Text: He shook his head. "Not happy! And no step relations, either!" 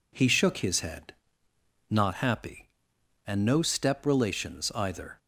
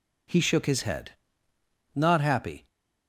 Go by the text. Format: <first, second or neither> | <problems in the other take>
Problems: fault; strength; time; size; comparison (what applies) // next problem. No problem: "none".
first | stops before "And no step relations either"; at 2.6 s